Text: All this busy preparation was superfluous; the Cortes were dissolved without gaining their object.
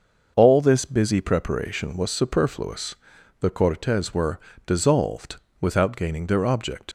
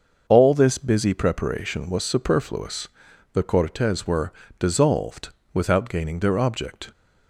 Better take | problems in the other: second | starts louder than the rest; noticeable; until 1.3 s; 6 dB; also in the second // pauses between "were" and "dissolved"; slight; at 4.3 s; 0.26 s long; slight in the second // pauses between "dissolved" and "without"; slight; at 5.3 s; 0.24 s long; slight in the second // leaves "object" unfinished; at 6.8 s; 65 ms

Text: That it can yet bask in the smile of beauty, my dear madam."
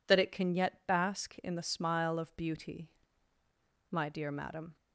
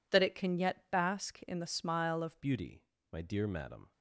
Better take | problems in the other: first | changes voice at "beauty"; from 2.4 s on; 1.5 s long

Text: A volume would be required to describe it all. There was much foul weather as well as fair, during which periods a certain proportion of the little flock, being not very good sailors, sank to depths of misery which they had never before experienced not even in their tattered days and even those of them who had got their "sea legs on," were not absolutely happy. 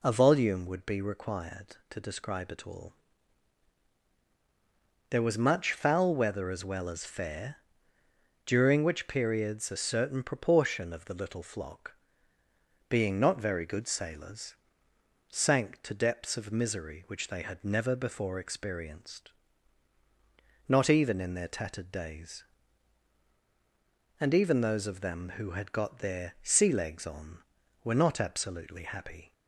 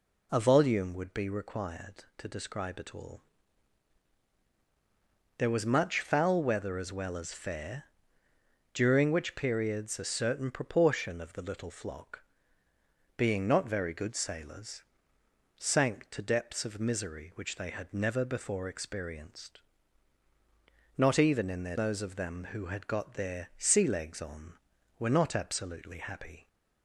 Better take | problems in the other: first | pauses between "experienced" and "not"; strong; at 19.5 s; 1.3 s long; strong in the first // skips "tattered days and even"; at 21.7 s

